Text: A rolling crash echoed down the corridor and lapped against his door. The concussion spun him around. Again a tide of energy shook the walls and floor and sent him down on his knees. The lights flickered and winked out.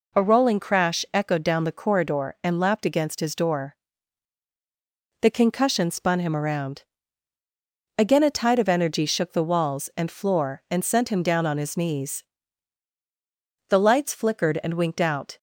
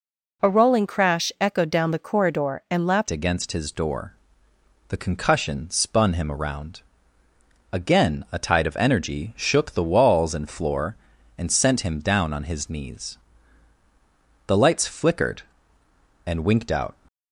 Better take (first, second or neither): first